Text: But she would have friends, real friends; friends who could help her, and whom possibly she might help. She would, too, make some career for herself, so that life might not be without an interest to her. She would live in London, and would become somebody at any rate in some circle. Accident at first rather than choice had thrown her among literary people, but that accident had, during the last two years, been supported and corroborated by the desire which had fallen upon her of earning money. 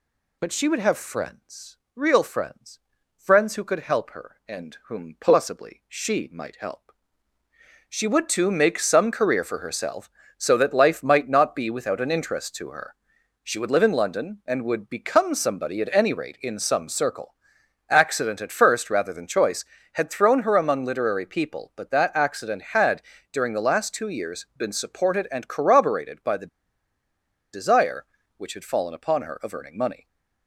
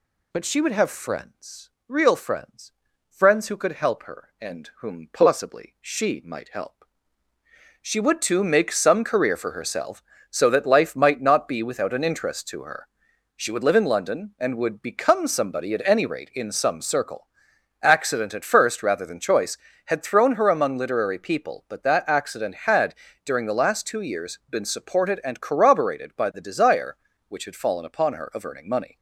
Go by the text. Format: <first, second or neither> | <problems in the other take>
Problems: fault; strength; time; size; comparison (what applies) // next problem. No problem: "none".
second | pauses between "the" and "desire"; at 26.4 s; 1.0 s long